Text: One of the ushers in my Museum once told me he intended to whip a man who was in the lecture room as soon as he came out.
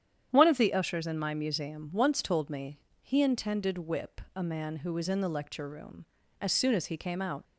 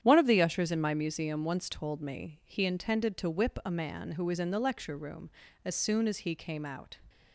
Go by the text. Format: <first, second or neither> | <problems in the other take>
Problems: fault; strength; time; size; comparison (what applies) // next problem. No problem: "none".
second | starts louder than the rest; strong; until 1.3 s; 9.5 dB; strong in the second // pauses between "me" and "he"; slight; at 2.7 s; 0.22 s long // skips "to"; at 3.7 s